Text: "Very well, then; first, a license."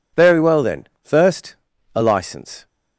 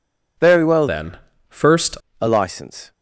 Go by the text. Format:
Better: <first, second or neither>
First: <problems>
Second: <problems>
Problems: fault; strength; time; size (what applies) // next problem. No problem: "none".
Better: first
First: none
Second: changes voice from "then" to "first"; from 0.8 to 1.9 s; 1.1 s long